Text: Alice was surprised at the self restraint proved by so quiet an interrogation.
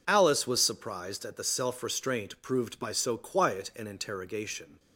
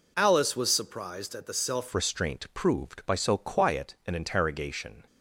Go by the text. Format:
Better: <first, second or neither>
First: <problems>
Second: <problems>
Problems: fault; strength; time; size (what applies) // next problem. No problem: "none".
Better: first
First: none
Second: changes voice at "restraint"; from 1.9 s on; 3.1 s long